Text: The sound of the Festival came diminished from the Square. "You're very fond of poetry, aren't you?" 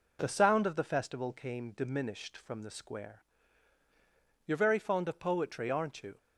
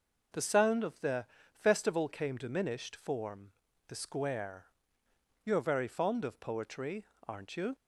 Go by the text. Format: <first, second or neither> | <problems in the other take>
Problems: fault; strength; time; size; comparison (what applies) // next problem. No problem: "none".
first | pauses between "the" and "Festival"; slight; at 1.2 s; 0.28 s long // says "form" for "from"; at 2.9 s